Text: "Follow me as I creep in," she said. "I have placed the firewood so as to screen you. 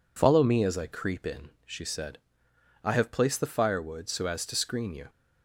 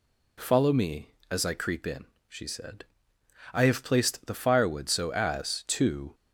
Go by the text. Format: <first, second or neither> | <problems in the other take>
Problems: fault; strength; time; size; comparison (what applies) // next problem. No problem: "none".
first | stops before "screen you"; at 6.1 s